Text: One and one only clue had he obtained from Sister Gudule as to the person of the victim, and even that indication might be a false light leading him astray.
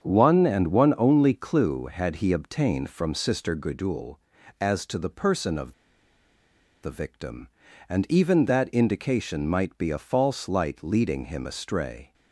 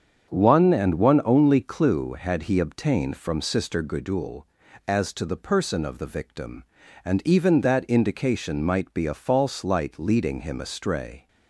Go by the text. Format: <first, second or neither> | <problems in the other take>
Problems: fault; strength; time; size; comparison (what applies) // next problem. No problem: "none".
second | starts louder than the rest; strong; until 1.0 s; 7.5 dB; strong in the second // pauses between "of" and "the"; at 5.7 s; 1.0 s long